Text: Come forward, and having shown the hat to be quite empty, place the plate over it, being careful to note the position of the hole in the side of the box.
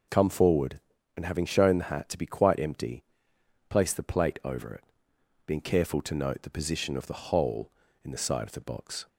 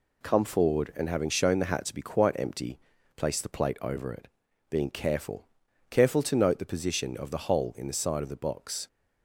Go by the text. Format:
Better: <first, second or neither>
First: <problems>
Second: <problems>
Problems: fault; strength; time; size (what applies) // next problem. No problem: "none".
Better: first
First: none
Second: says "careful" twice; at 5.8 s